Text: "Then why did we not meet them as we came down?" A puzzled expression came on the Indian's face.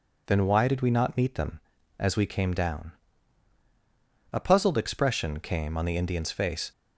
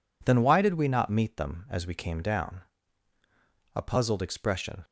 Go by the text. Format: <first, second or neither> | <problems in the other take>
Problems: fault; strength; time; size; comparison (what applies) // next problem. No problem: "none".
first | stops before "came on the Indian's face"; at 4.8 s